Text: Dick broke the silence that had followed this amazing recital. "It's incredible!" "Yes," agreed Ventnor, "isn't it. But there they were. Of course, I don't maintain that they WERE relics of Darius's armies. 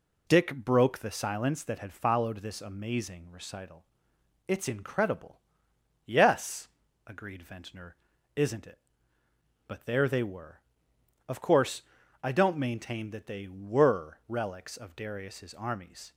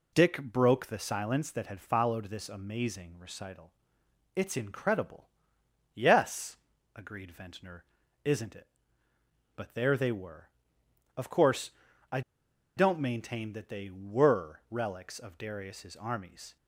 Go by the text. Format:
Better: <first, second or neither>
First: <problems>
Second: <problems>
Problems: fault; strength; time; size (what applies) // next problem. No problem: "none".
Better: first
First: none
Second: pauses between "I" and "don't"; noticeable; at 12.2 s; 0.55 s long